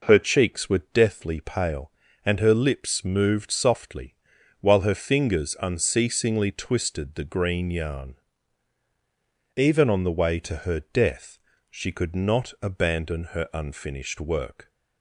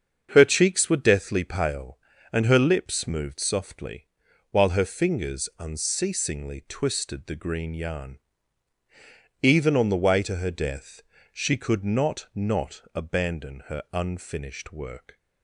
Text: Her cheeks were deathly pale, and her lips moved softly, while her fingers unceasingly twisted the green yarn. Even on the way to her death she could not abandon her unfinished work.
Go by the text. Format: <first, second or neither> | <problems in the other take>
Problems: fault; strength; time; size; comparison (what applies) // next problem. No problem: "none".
first | starts louder than the rest; until 1.3 s; 7 dB // pauses between "death" and "she"; slight; at 11.0 s; 0.30 s long; slight in the first // says "not" twice; at 12.3 s